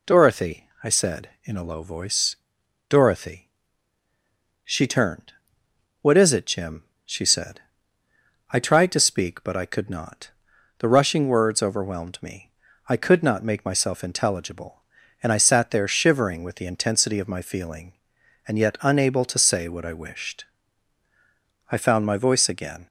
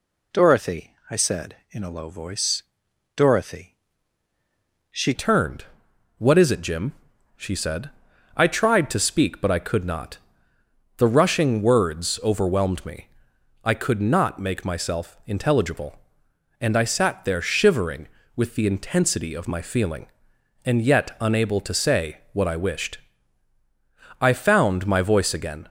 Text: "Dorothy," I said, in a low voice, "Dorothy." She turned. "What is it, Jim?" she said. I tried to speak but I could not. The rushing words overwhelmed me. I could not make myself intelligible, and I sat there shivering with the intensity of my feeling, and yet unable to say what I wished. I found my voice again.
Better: first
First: none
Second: changes voice at "turned"; from 5.1 s on; 20.5 s long

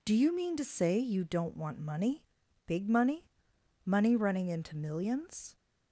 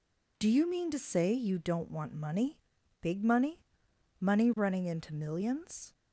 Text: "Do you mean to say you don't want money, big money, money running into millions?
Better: neither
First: none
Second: none

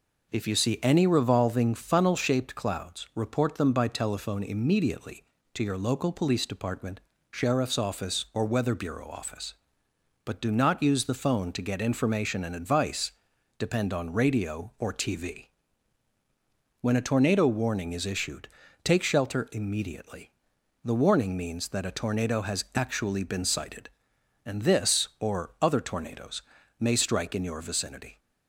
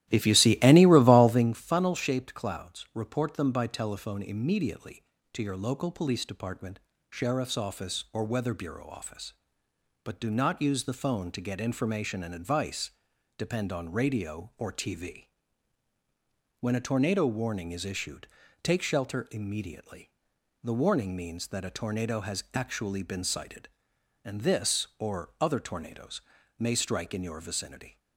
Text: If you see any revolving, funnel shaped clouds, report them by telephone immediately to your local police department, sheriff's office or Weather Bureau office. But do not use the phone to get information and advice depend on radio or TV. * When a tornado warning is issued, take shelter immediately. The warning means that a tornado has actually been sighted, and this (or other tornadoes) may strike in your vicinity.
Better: first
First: pauses between "advice" and "depend"; at 13.1 s; 0.44 s long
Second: starts louder than the rest; strong; until 1.6 s; 14.5 dB // pauses between "advice" and "depend"; at 12.9 s; 0.44 s long

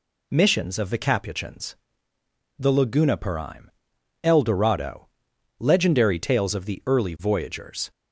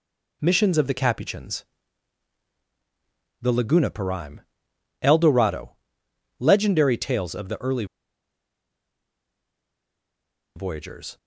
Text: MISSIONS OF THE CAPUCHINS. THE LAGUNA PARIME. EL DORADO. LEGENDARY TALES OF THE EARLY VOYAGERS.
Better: first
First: none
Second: pauses between "EARLY" and "VOYAGERS"; strong; at 7.8 s; 2.7 s long

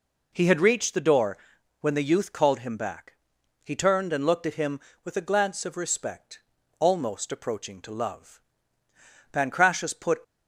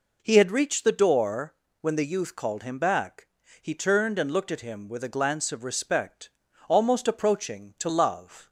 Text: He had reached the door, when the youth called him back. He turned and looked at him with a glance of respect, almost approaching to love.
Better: second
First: goes on to say "Pancratius put"; noticeable; from 9.3 s on; 0.88 s long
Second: none

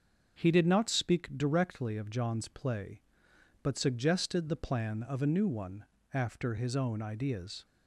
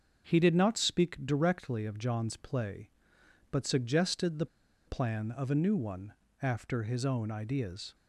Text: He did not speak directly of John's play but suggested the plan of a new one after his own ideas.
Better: first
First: starts louder than the rest; until 1.3 s; 6.5 dB // pauses between "one" and "after"; slight; at 5.8 s; 0.26 s long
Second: starts louder than the rest; until 1.2 s; 6.5 dB // pauses between "the" and "plan"; at 4.4 s; 0.41 s long // pauses between "one" and "after"; slight; at 6.1 s; 0.26 s long

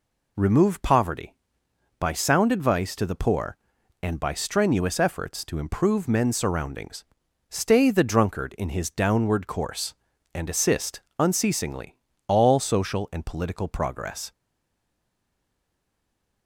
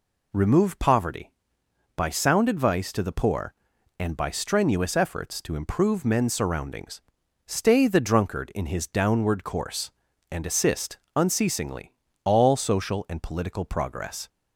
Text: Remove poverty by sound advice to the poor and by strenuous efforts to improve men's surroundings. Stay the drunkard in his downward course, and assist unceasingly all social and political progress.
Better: second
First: pauses between "assist" and "unceasingly"; slight; at 11.0 s; 0.18 s long // pauses between "unceasingly" and "all"; slight; at 11.9 s; 0.32 s long // stays silent after the last word; from 14.3 s on; 2.1 s long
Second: pauses between "assist" and "unceasingly"; slight; at 10.9 s; 0.18 s long // pauses between "unceasingly" and "all"; slight; at 11.9 s; 0.32 s long

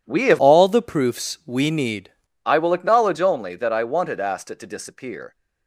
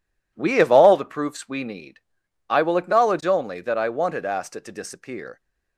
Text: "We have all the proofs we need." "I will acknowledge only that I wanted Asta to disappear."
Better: second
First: changes voice from "all" to "need"; from 0.3 to 2.1 s; 1.8 s long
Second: none

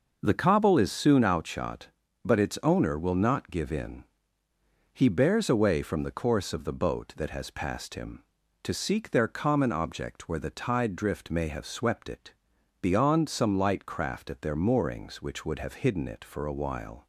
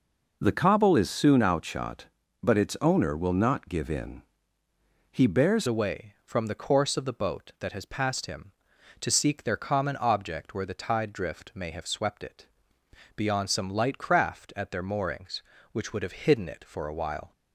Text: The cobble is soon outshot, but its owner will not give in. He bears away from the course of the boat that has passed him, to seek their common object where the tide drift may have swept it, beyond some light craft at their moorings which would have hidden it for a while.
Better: first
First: none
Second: changes voice at "away"; from 5.6 s on; 11.7 s long

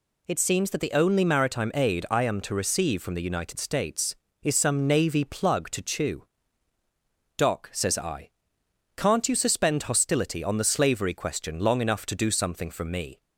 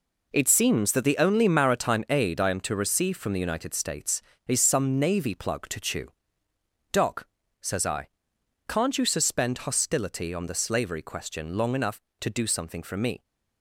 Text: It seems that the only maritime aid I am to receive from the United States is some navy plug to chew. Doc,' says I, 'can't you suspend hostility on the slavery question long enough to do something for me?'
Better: first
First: none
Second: gets quieter; strong; throughout; 9.5 dB

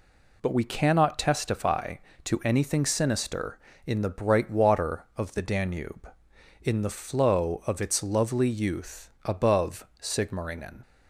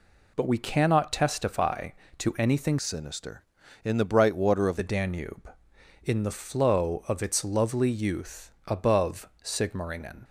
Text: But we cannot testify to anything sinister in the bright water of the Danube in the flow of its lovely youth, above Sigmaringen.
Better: first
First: pauses between "above" and "Sigmaringen"; slight; at 9.8 s; 0.16 s long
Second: changes voice from "sinister" to "of"; from 2.7 to 4.7 s; 2.0 s long // pauses between "above" and "Sigmaringen"; slight; at 9.2 s; 0.16 s long

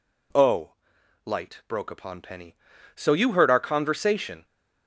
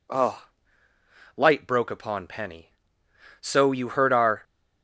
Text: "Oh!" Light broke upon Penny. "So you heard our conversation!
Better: first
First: none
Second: stops before "conversation"; at 4.4 s

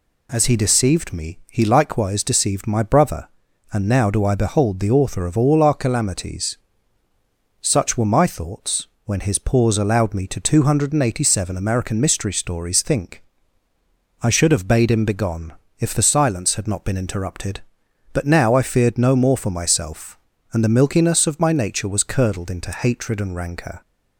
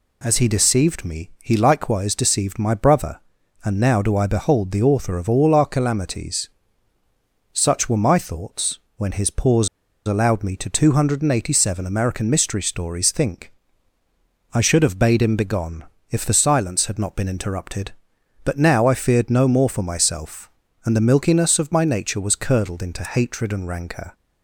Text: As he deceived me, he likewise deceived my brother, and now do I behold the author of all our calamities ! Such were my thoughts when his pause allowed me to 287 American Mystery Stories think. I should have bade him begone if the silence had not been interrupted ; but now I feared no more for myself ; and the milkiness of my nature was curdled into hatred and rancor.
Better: first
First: pauses between "thoughts" and "when"; slight; at 8.8 s; 0.20 s long // pauses between "begone" and "if"; slight; at 15.5 s; 0.24 s long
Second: pauses between "thoughts" and "when"; slight; at 8.7 s; 0.20 s long // pauses between "pause" and "allowed"; at 9.6 s; 0.37 s long // pauses between "begone" and "if"; slight; at 15.8 s; 0.24 s long

